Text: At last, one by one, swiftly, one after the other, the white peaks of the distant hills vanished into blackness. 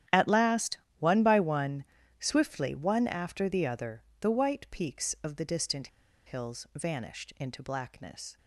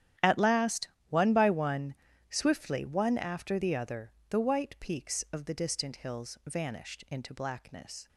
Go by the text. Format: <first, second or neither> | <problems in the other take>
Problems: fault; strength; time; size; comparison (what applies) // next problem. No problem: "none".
second | starts louder than the rest; strong; until 1.3 s; 10.5 dB; strong in the second // pauses between "distant" and "hills"; at 5.8 s; 0.37 s long